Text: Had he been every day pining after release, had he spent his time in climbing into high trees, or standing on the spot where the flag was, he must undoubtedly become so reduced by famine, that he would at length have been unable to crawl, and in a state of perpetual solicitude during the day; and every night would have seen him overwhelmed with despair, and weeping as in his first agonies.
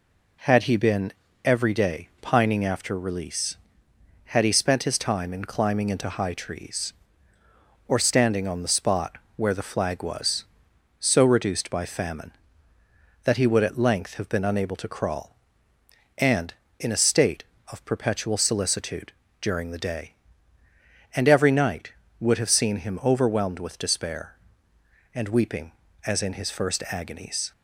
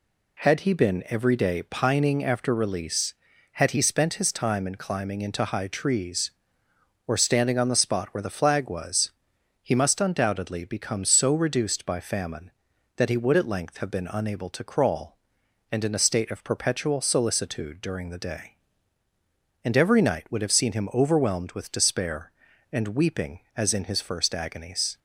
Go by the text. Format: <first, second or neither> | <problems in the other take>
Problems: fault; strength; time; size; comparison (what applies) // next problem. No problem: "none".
second | pauses between "been" and "every"; slight; at 1.1 s; 0.32 s long // pauses between "spot" and "where"; slight; at 9.1 s; 0.16 s long // skips "he must undoubtedly become"; at 10.7 s // pauses between "solicitude" and "during"; slight; at 19.1 s; 0.30 s long